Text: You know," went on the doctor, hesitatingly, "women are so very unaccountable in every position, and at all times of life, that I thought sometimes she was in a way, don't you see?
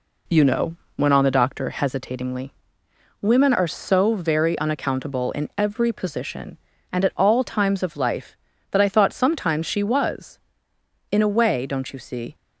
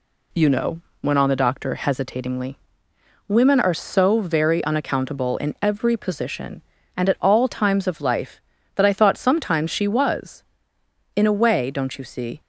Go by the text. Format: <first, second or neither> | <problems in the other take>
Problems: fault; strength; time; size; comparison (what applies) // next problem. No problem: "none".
second | starts louder than the rest; slight; until 1.6 s; 2.5 dB